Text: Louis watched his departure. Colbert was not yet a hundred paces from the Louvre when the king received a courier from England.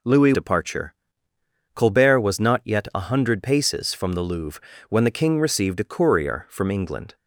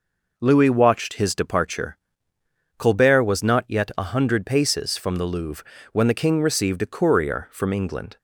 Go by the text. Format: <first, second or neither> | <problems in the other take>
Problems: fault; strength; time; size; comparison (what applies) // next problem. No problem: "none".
second | skips "watched his"; at 0.3 s // pauses between "Louvre" and "when"; slight; at 4.6 s; 0.28 s long; slight in the second